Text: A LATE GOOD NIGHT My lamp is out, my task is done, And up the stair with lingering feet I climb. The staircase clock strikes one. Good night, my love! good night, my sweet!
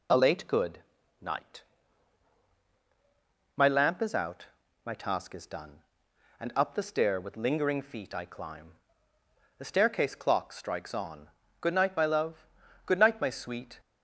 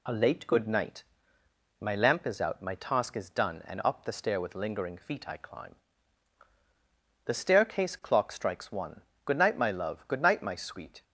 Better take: second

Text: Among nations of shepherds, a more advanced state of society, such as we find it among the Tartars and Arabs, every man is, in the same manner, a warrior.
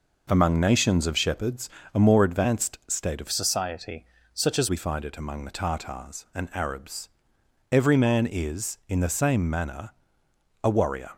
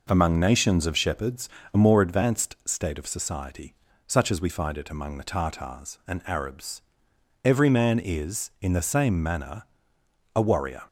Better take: second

